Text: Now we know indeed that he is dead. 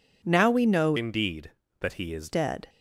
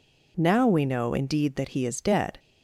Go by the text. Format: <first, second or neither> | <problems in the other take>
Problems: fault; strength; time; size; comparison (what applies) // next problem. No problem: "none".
second | changes voice from "indeed" to "is"; from 0.9 to 2.3 s; 1.4 s long